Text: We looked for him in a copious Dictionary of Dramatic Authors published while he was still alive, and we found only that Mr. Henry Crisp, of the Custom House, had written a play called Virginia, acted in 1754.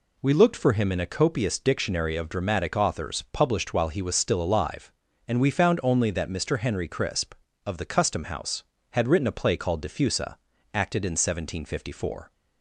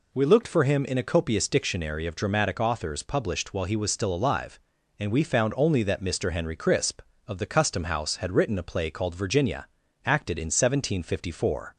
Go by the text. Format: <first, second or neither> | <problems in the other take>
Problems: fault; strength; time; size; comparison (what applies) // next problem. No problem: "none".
second | says "Diffusa" for "Virginia"; at 9.8 s